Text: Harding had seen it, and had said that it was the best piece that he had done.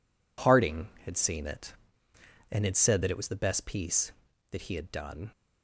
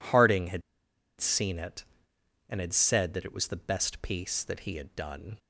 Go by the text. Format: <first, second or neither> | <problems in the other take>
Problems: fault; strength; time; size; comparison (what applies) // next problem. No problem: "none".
first | pauses between "had" and "seen"; noticeable; at 0.6 s; 0.58 s long